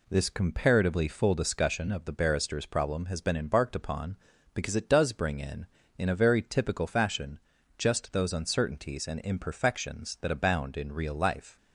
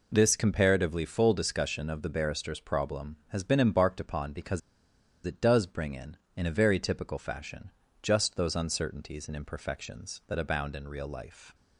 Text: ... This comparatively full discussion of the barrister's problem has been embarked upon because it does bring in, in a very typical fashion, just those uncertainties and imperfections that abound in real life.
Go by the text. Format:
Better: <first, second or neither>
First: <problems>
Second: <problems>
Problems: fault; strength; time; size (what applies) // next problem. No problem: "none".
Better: first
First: none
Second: pauses between "because" and "it"; noticeable; at 4.6 s; 0.64 s long